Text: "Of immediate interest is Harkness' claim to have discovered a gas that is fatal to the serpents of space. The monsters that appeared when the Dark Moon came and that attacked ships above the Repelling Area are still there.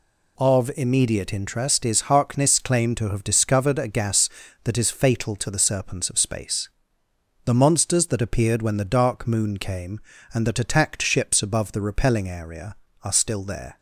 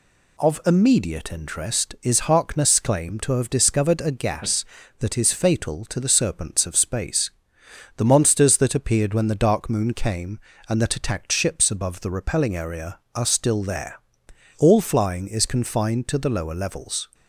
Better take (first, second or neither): first